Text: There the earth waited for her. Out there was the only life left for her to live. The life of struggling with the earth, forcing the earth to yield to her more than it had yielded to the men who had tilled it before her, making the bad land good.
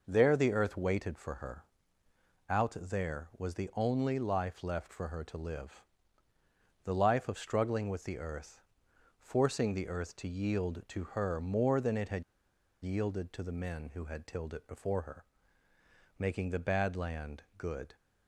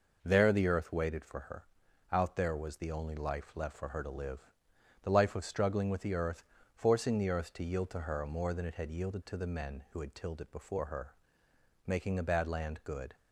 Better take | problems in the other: second | pauses between "had" and "yielded"; noticeable; at 12.2 s; 0.61 s long

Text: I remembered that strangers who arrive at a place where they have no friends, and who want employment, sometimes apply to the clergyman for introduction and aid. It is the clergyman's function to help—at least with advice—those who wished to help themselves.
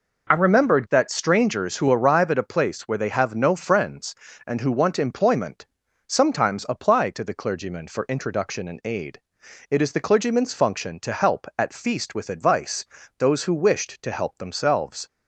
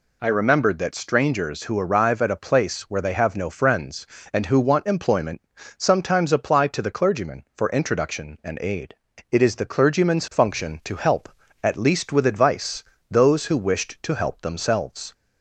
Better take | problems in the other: second | says "feast" for "least"; at 11.7 s

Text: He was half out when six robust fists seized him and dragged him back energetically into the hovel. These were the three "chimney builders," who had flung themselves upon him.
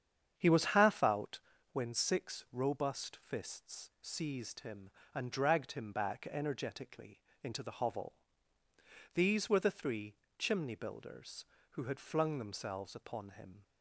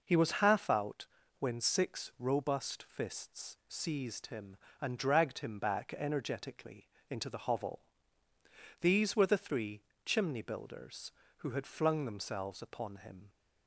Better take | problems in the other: second | starts louder than the rest; strong; until 1.7 s; 8 dB // pauses between "out" and "when"; slight; at 1.3 s; 0.34 s long; slight in the second // pauses between "energetically" and "into"; slight; at 7.2 s; 0.22 s long; slight in the second // pauses between "three" and "chimney"; slight; at 10.1 s; 0.22 s long; slight in the second

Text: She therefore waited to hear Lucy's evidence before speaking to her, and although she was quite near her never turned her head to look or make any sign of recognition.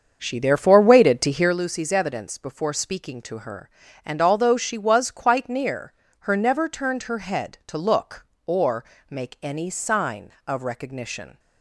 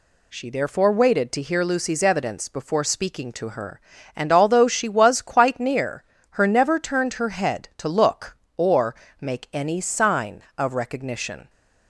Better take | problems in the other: second | starts louder than the rest; until 1.6 s; 7 dB // pauses between "near" and "her"; slight; at 5.9 s; 0.30 s long; slight in the second // pauses between "or" and "make"; slight; at 8.8 s; 0.24 s long; slight in the second

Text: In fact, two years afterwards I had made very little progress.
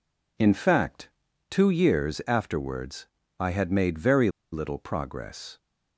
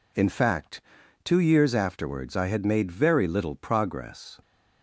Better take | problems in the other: second | pauses between "afterwards" and "I"; slight; at 3.0 s; 0.32 s long // pauses between "very" and "little"; slight; at 4.2 s; 0.23 s long

